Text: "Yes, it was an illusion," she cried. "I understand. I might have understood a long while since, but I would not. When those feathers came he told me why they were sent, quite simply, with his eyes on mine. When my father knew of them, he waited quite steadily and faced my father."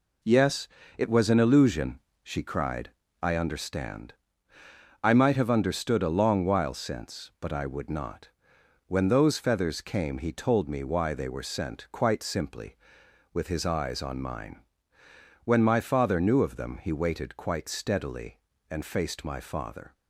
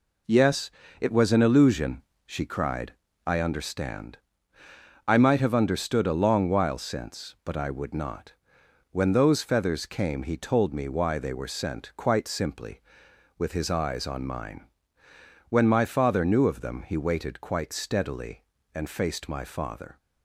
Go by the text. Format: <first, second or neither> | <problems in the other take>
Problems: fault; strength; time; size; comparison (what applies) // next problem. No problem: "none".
neither | none